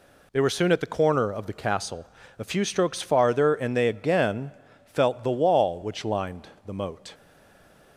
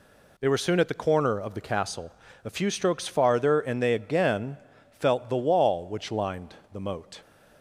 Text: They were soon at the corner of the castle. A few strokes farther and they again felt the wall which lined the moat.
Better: second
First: pauses between "again" and "felt"; at 4.5 s; 0.42 s long // pauses between "lined" and "the"; slight; at 6.4 s; 0.18 s long // stays silent after the last word; slight; from 7.1 s on; 0.8 s long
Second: pauses between "again" and "felt"; at 4.5 s; 0.42 s long // pauses between "lined" and "the"; slight; at 6.5 s; 0.18 s long

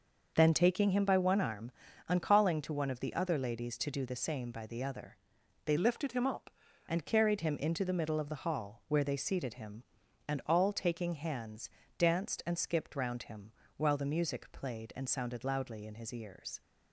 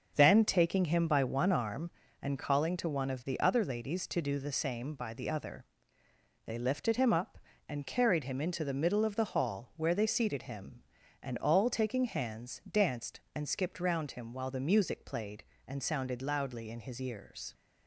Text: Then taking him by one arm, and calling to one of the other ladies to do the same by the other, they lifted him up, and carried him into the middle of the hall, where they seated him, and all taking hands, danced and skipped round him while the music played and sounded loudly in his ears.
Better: second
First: starts louder than the rest; noticeable; until 1.3 s; 6 dB // changes voice from "lifted" to "up"; from 5.7 to 6.5 s; 0.8 s long // pauses between "him" and "while"; slight; at 13.5 s; 0.26 s long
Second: starts louder than the rest; until 1.1 s; 6.5 dB

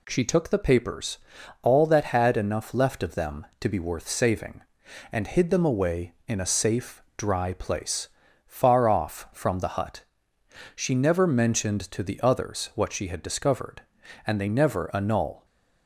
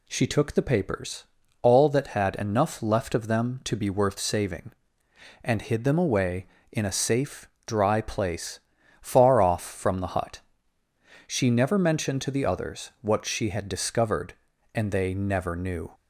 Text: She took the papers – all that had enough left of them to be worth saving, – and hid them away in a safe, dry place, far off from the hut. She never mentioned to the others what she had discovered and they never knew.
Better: second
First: says "annul" for "knew"; at 14.9 s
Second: none

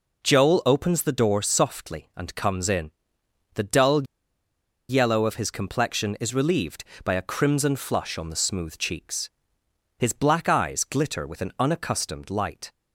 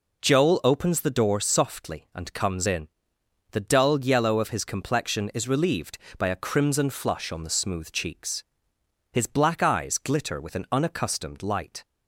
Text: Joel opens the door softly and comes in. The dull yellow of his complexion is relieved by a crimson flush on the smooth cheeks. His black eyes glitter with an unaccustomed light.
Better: second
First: pauses between "dull" and "yellow"; noticeable; at 4.0 s; 0.83 s long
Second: none

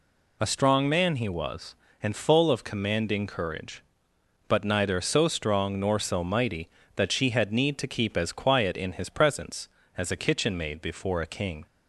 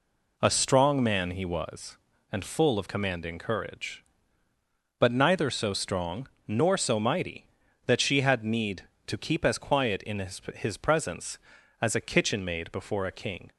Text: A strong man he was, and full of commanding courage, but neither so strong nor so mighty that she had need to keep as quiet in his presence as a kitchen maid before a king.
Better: first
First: none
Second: pauses between "strong" and "nor"; slight; at 6.2 s; 0.18 s long // says "his" twice; at 10.5 s

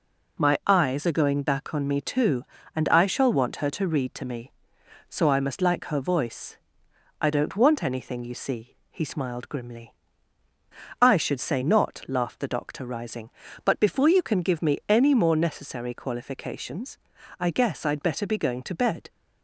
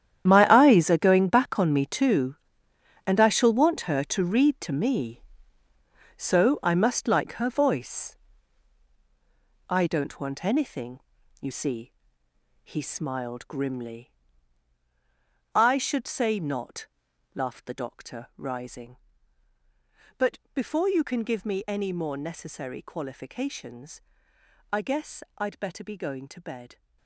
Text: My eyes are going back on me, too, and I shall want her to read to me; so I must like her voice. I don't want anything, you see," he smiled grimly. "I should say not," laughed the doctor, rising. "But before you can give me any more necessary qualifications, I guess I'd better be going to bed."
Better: first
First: none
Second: gets quieter; strong; throughout; 13.5 dB // pauses between "But" and "before"; slight; at 20.3 s; 0.16 s long

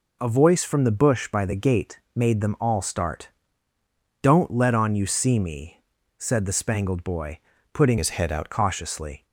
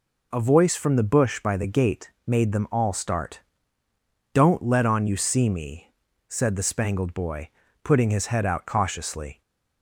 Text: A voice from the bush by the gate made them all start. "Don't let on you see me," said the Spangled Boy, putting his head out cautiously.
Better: second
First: changes voice from "his" to "out"; from 7.9 to 8.5 s; 0.6 s long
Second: none

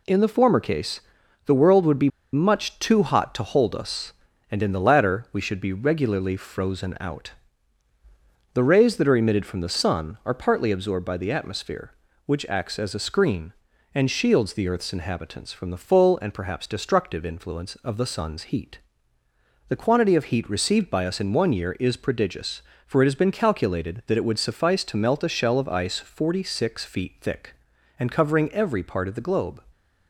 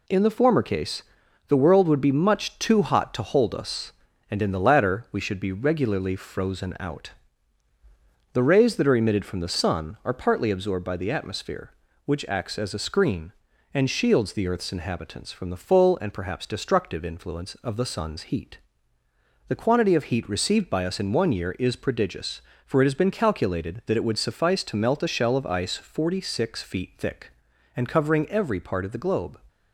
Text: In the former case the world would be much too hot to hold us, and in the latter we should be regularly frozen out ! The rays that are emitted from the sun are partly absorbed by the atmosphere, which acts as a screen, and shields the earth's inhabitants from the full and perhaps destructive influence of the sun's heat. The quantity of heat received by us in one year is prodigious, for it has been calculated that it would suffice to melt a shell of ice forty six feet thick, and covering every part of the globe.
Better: second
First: pauses between "case" and "the"; noticeable; at 0.9 s; 0.46 s long // pauses between "be" and "much"; slight; at 2.0 s; 0.23 s long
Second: pauses between "case" and "the"; noticeable; at 1.0 s; 0.46 s long

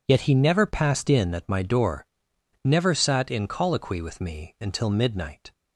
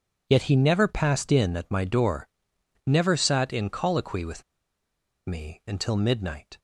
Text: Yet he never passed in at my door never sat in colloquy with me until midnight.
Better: first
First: pauses between "door" and "never"; noticeable; at 2.0 s; 0.58 s long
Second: pauses between "door" and "never"; noticeable; at 2.2 s; 0.58 s long // pauses between "with" and "me"; noticeable; at 4.4 s; 0.83 s long

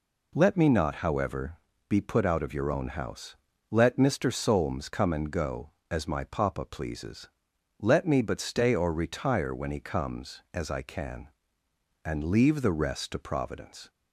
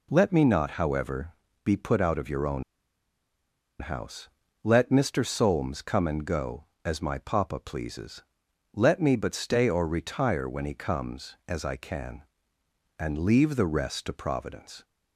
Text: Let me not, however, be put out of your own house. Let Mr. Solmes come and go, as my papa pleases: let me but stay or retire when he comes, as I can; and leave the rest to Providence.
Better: first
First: none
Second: pauses between "own" and "house"; at 2.6 s; 1.1 s long

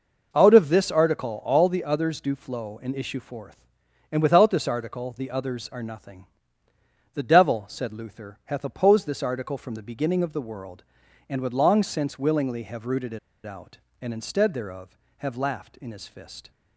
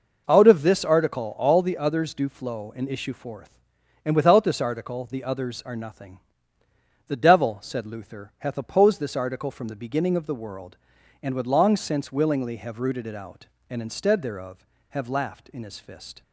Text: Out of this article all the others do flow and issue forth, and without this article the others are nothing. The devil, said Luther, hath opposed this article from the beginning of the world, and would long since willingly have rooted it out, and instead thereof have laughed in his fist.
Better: second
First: pauses between "it" and "out"; slight; at 13.1 s; 0.27 s long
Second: none

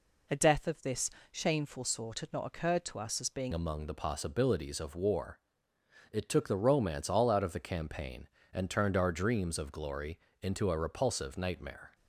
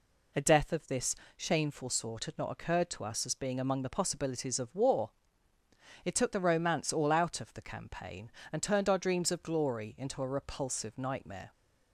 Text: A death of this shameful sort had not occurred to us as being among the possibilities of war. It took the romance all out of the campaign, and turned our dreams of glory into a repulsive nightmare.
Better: second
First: pauses between "this" and "shameful"; slight; at 1.0 s; 0.20 s long // changes voice at "among"; from 3.5 s on; 8.4 s long // pauses between "glory" and "into"; slight; at 10.1 s; 0.22 s long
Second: pauses between "this" and "shameful"; slight; at 1.1 s; 0.20 s long

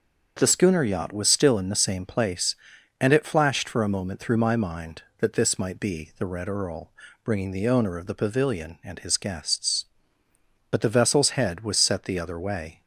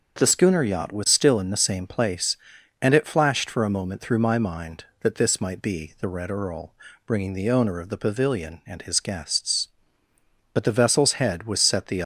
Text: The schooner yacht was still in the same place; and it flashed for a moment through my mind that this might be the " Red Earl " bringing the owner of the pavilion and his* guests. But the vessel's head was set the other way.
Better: first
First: starts louder than the rest; until 1.3 s; 7 dB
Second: starts louder than the rest; until 1.2 s; 6.5 dB // stops before "other way"; at 12.0 s

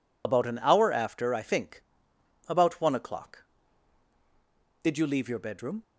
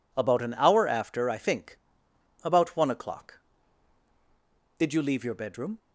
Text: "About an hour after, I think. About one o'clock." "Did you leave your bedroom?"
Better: second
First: loses the start of "About"; at 0.2 s; 65 ms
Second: none

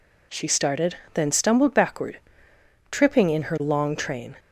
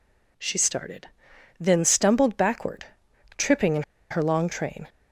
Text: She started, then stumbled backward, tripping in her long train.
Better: first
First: none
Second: pauses between "in" and "her"; slight; at 3.8 s; 0.28 s long

